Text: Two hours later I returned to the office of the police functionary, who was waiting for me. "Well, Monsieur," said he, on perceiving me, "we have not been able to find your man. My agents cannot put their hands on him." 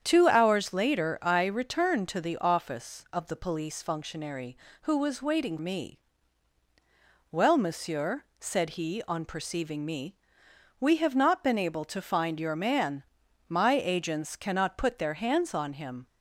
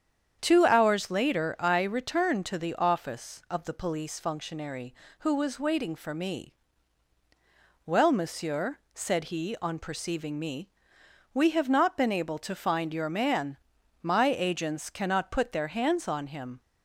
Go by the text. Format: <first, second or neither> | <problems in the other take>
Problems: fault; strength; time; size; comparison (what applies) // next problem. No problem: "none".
second | starts louder than the rest; strong; until 1.0 s; 8.5 dB; strong in the second // skips "for"; at 5.5 s